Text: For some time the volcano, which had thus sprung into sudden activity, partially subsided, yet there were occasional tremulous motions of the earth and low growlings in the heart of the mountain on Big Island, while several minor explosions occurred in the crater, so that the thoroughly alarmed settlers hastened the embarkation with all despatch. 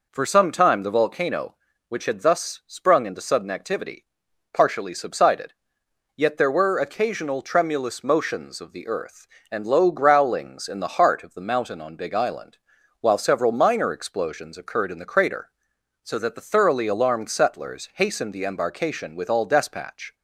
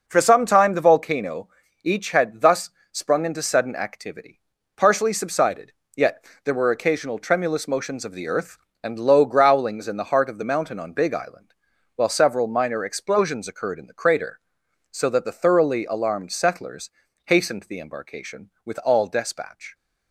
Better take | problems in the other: first | says "each" for "which"; at 1.8 s // pauses between "thus" and "sprung"; slight; at 2.7 s; 0.22 s long // pauses between "yet" and "there"; slight; at 6.2 s; 0.20 s long // pauses between "settlers" and "hastened"; slight; at 16.9 s; 0.36 s long

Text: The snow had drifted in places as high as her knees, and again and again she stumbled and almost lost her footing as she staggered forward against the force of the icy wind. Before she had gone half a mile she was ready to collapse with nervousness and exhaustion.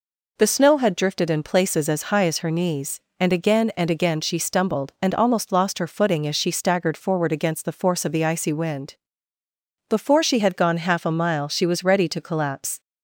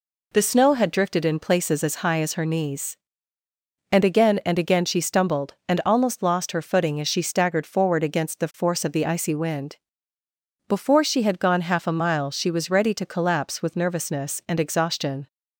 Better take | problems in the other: second | stops before "with nervousness and exhaustion"; at 12.8 s

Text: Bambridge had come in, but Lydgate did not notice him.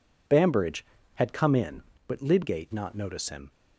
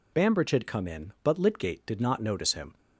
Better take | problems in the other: second | skips "did"; at 2.7 s

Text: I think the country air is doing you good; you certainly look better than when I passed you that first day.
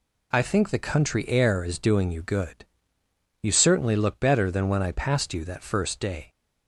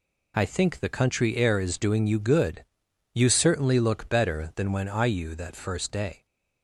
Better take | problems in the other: first | skips "passed"; at 5.0 s

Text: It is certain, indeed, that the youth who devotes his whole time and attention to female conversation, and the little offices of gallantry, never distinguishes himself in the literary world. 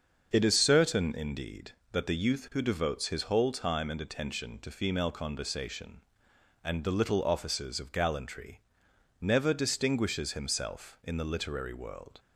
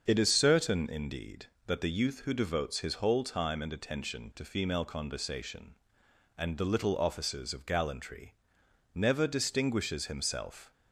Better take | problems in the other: first | starts louder than the rest; until 1.0 s; 7 dB; also in the first // stops before "in the literary world"; at 10.7 s

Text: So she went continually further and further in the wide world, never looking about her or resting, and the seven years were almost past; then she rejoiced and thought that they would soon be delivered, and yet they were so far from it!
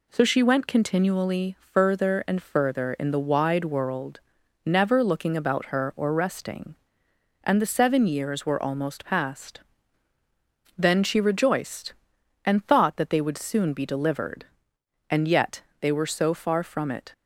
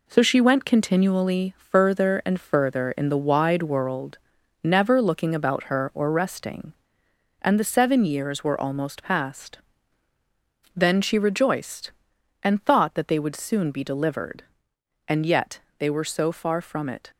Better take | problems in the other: first | gets quieter; noticeable; throughout; 6 dB // pauses between "yet" and "they"; slight; at 15.5 s; 0.20 s long; slight in the first

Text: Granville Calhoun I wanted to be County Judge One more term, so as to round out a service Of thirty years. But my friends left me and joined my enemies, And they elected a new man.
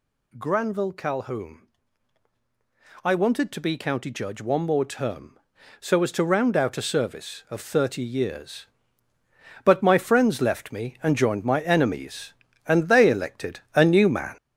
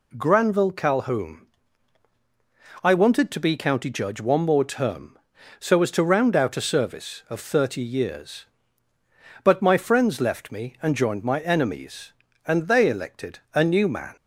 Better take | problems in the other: second | gets louder; throughout; 6.5 dB // pauses between "Calhoun" and "I"; strong; at 1.6 s; 1.3 s long; strong in the second // pauses between "elected" and "a"; slight; at 13.5 s; 0.16 s long; slight in the second

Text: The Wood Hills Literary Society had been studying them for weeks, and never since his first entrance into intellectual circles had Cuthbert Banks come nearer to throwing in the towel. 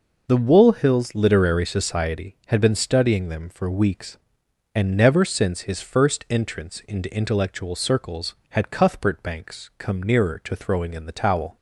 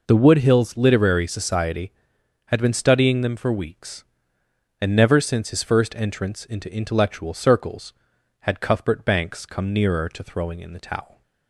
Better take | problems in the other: second | says "Wool" for "Wood"; at 0.3 s

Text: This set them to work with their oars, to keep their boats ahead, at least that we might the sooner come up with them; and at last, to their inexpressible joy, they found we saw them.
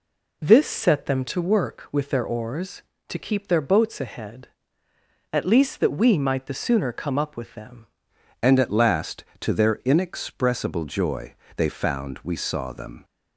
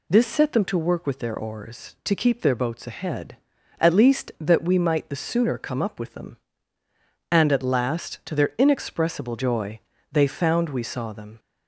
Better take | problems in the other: second | changes voice at "and"; from 8.4 s on; 4.6 s long

